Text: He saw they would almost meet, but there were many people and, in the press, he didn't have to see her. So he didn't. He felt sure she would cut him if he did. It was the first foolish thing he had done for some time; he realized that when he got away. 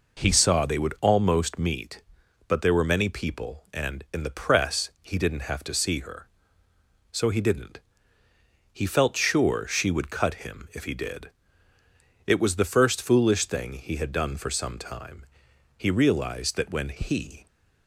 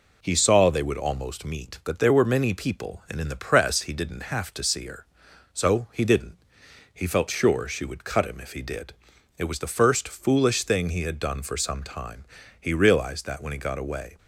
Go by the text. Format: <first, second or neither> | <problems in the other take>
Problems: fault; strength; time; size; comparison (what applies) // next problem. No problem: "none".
second | stops before "got away"; at 17.4 s